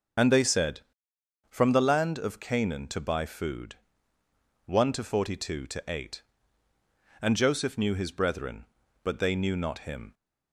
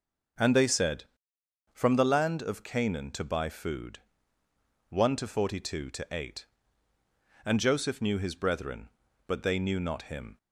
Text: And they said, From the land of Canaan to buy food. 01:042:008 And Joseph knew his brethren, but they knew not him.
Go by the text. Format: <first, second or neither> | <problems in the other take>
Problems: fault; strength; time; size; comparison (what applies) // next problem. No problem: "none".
second | loses the start of "And"; at 0.1 s; 40 ms